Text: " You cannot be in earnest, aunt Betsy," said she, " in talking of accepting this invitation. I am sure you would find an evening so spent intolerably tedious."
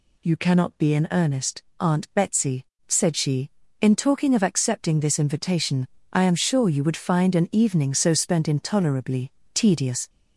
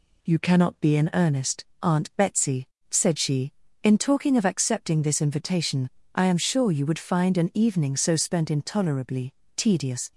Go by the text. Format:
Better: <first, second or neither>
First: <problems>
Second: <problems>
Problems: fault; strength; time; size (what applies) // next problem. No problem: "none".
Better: second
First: gets louder; noticeable; throughout; 6 dB // pauses between "intolerably" and "tedious"; slight; at 9.3 s; 0.22 s long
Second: pauses between "intolerably" and "tedious"; slight; at 9.3 s; 0.22 s long